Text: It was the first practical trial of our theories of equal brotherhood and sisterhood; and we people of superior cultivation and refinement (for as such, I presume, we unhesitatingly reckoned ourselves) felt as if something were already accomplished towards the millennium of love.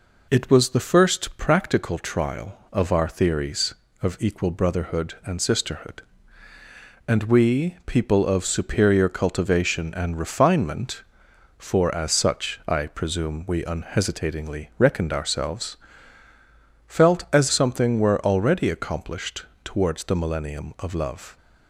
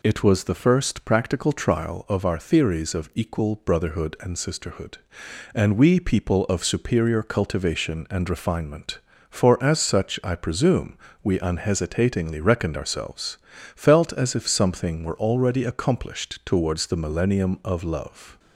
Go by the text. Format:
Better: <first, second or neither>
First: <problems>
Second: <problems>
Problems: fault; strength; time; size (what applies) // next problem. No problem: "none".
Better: second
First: skips "if"; at 17.5 s // pauses between "accomplished" and "towards"; slight; at 19.4 s; 0.20 s long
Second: none